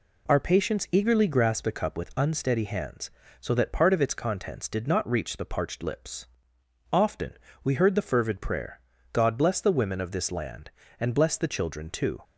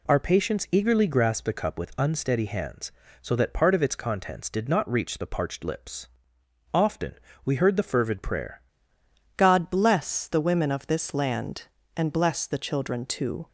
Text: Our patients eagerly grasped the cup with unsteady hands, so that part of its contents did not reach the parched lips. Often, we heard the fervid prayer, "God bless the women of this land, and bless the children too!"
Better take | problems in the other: first | changes voice at "God"; from 9.3 s on; 4.1 s long

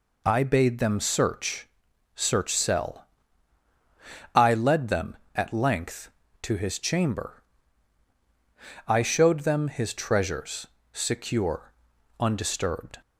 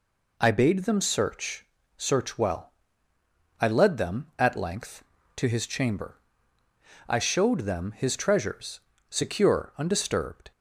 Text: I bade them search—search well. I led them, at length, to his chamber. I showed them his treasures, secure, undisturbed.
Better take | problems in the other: second | says "cell" for "well"; at 2.5 s

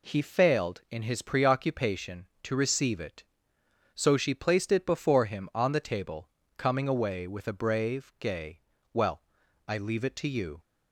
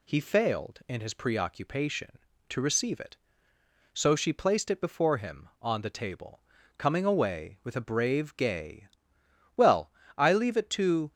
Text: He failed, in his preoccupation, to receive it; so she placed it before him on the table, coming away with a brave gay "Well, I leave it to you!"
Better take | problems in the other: first | pauses between "gay" and "Well"; noticeable; at 8.8 s; 0.66 s long; slight in the first // stops before "you"; at 11.1 s

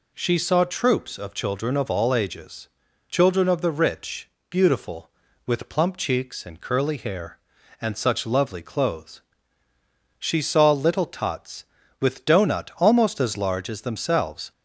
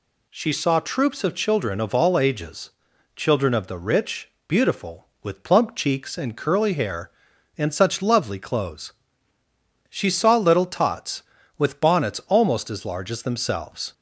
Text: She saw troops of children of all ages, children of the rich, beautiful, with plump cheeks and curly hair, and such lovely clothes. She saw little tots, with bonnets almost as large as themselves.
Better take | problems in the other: second | says "doughnut" for "bonnets"; at 12.2 s

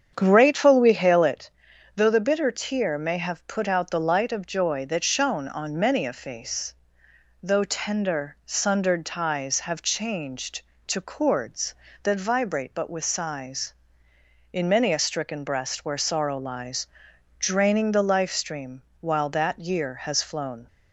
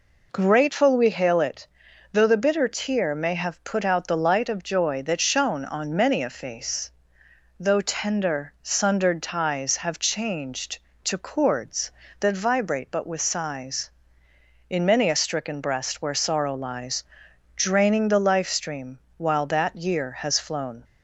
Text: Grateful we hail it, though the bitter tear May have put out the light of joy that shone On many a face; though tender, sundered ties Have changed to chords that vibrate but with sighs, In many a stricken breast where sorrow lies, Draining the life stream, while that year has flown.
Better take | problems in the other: second | starts louder than the rest; strong; until 1.4 s; 8 dB

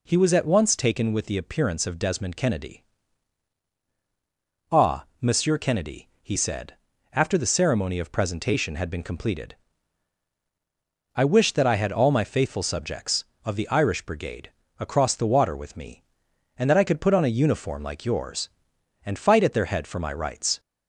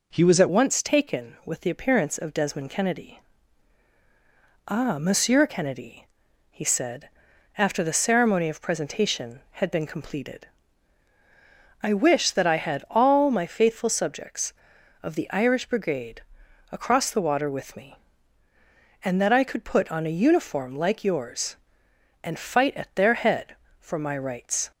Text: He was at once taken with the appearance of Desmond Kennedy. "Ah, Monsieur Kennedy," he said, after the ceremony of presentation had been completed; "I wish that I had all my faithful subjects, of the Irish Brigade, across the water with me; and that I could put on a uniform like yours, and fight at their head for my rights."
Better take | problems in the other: first | changes voice at "once"; from 0.4 s on; 24.3 s long

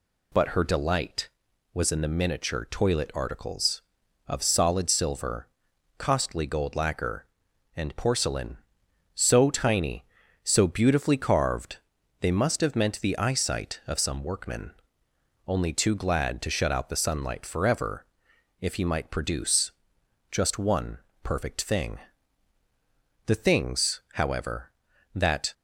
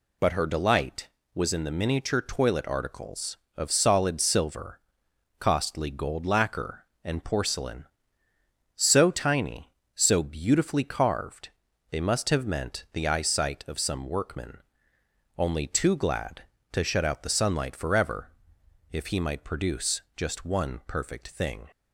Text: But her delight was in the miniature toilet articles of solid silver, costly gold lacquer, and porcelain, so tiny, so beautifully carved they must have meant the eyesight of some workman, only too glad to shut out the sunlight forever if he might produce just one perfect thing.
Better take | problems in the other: second | pauses between "carved" and "they"; at 11.7 s; 0.44 s long; also in the second // pauses between "forever" and "if"; noticeable; at 18.0 s; 0.56 s long; noticeable in the second // pauses between "produce" and "just"; noticeable; at 19.7 s; 0.60 s long; slight in the second // pauses between "one" and "perfect"; slight; at 20.9 s; 0.26 s long // goes on to say "The things however that"; strong; from 23.2 s on; 2.2 s long

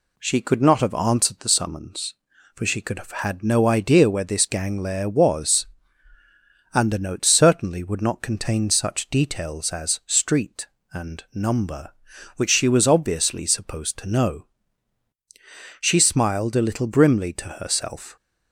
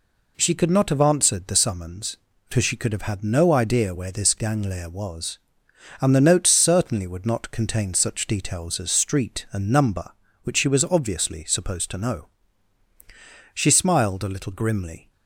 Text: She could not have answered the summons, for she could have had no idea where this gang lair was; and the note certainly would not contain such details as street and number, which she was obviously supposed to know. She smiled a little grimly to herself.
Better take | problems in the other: first | stops before "to herself"; at 15.0 s

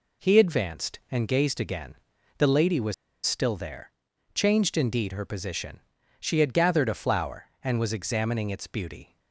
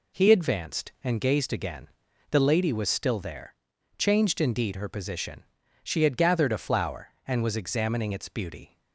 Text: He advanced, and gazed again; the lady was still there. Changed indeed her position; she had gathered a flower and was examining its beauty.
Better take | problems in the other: second | pauses between "was" and "still"; slight; at 2.9 s; 0.32 s long

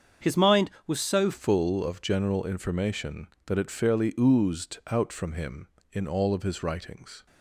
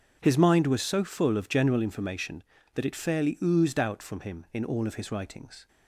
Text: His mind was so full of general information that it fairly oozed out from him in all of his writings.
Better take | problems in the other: second | starts louder than the rest; until 1.3 s; 7 dB; also in the second // changes voice at "full"; from 1.3 s on; 5.9 s long

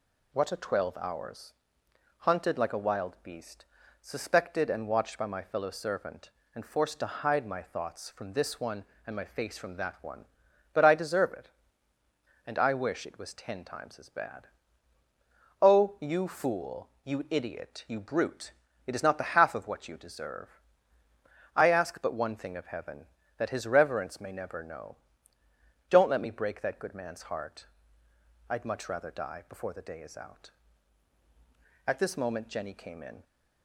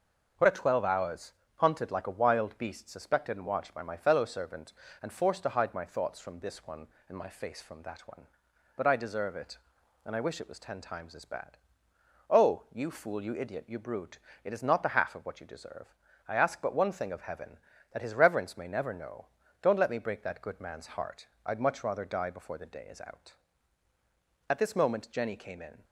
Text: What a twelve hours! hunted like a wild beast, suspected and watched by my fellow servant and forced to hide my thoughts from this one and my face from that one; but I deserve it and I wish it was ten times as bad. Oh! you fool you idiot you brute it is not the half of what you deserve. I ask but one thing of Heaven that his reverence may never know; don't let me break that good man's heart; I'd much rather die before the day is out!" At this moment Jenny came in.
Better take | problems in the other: neither | pauses between "brute" and "it"; slight; the same in both

